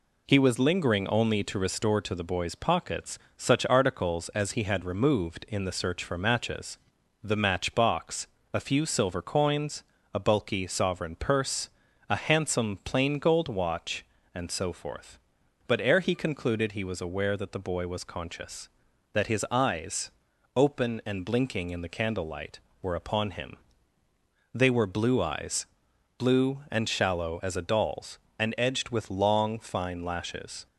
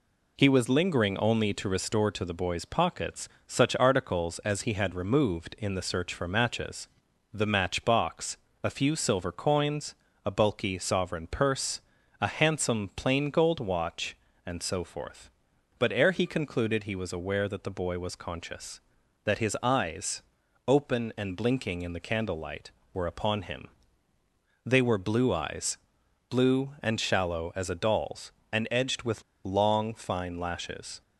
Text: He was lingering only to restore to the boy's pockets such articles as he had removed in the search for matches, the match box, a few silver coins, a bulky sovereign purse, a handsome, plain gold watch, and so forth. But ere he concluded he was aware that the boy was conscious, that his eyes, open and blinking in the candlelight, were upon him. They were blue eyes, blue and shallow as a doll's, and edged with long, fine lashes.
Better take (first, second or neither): first